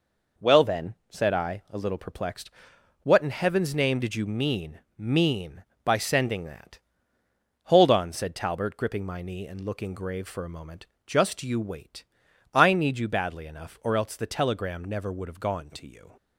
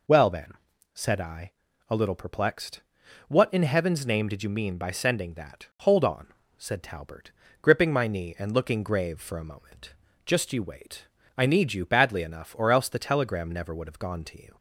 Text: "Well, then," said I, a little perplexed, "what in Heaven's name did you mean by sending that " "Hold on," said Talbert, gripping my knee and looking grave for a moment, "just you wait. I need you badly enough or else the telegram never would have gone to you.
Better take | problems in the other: second | says "mean" twice; at 4.9 s

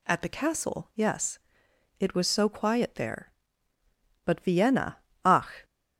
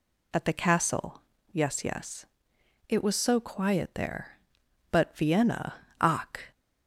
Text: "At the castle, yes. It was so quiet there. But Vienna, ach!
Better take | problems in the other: first | says "yes" twice; at 1.8 s

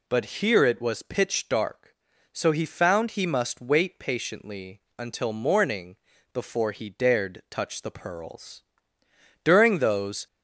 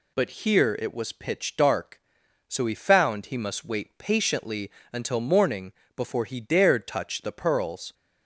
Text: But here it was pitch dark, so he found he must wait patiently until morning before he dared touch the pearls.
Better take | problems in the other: second | pauses between "But" and "here"; slight; at 0.2 s; 0.16 s long // pauses between "patiently" and "until"; slight; at 4.8 s; 0.18 s long; slight in the second // pauses between "morning" and "before"; slight; at 5.9 s; 0.36 s long; slight in the second // goes on to say "During those"; noticeable; from 9.4 s on; 0.82 s long

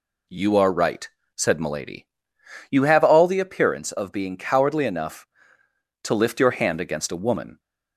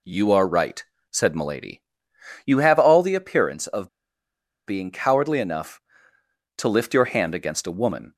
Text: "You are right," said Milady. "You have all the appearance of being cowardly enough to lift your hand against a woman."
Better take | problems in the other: first | pauses between "of" and "being"; noticeable; at 3.8 s; 0.80 s long

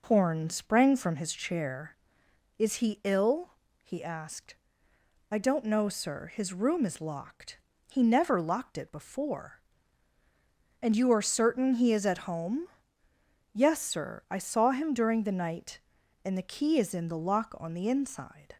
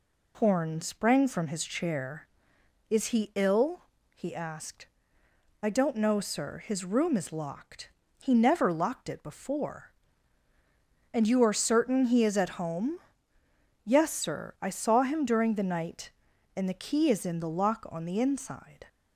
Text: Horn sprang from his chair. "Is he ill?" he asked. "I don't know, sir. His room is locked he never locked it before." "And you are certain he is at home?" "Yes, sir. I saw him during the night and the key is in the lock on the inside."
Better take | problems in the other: second | starts louder than the rest; noticeable; until 1.3 s; 5 dB // pauses between "locked" and "he"; slight; at 7.5 s; 0.28 s long; slight in the second

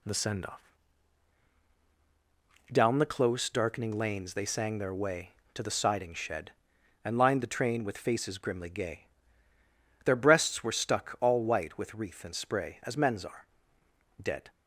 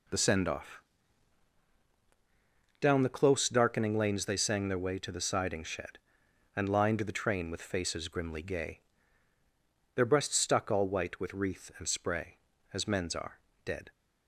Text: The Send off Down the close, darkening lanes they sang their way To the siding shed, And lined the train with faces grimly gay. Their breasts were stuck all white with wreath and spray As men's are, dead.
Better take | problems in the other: first | pauses between "off" and "Down"; strong; at 0.7 s; 2.0 s long; strong in the first // skips "were"; at 10.3 s

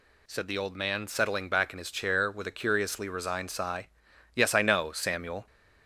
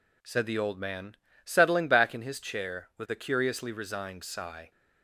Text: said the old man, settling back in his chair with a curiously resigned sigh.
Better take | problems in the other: second | goes on to say "Yes I know Samuel"; noticeable; from 4.3 s on; 1.1 s long

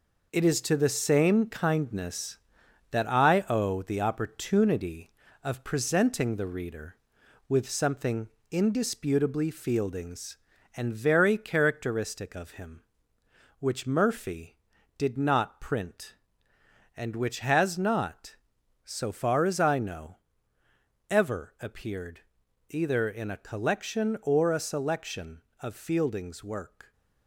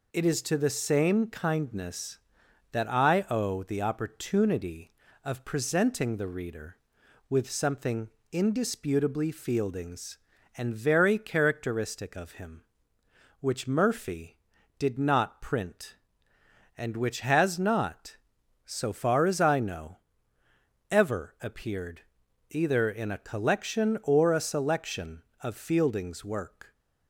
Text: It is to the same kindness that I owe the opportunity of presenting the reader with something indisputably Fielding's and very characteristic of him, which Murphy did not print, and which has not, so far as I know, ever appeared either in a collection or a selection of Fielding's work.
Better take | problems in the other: second | gets quieter; throughout; 6.5 dB // pauses between "something" and "indisputably"; slight; at 8.2 s; 0.22 s long; slight in the second // pauses between "appeared" and "either"; noticeable; at 22.1 s; 0.50 s long; noticeable in the second

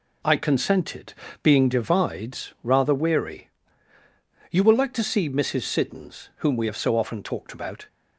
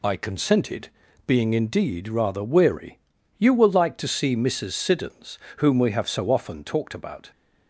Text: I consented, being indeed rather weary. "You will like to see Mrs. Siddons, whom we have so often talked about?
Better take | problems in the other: second | says "divides" for "indeed"; at 1.6 s

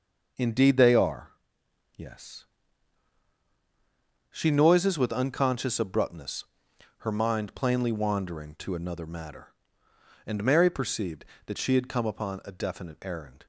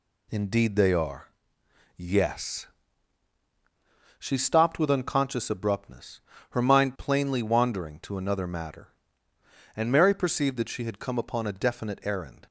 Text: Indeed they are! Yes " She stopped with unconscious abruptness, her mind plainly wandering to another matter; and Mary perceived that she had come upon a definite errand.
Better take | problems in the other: second | says "noises" for "stopped"; at 4.4 s

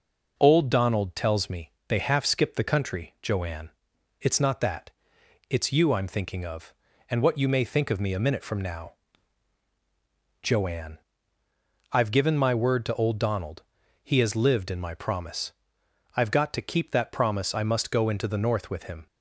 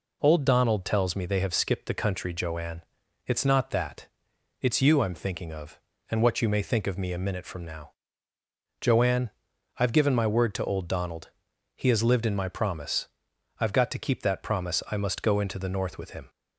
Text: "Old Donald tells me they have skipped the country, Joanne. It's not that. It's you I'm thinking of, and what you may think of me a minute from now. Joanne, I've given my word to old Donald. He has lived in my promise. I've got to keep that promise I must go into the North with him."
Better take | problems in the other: second | pauses between "me" and "they"; slight; at 1.7 s; 0.18 s long // says "half" for "have"; at 1.9 s

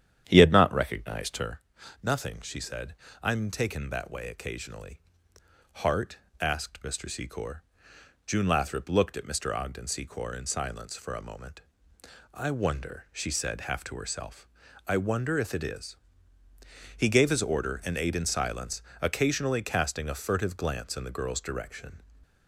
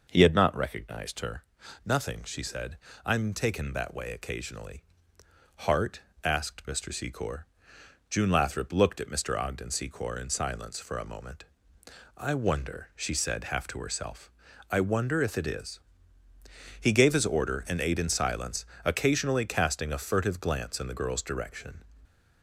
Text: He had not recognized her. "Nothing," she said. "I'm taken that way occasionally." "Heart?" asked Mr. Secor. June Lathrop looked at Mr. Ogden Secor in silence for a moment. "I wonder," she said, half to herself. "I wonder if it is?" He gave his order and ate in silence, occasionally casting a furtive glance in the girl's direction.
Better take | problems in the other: second | starts louder than the rest; strong; until 1.6 s; 9.5 dB // stays silent after the last word; slight; from 21.9 s on; 0.5 s long

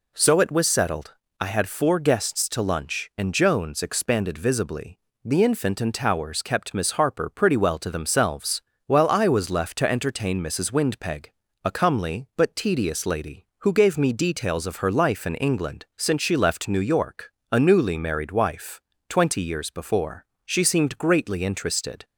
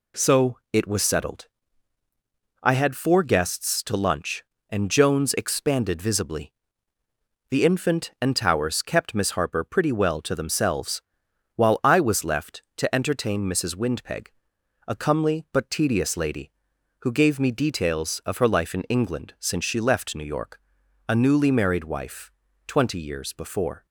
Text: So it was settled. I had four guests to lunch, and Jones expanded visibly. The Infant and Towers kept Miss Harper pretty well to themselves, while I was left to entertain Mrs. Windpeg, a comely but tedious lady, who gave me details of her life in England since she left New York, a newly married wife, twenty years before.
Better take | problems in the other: second | goes on to say "She seemed greatly interested"; from 20.4 s on; 1.6 s long

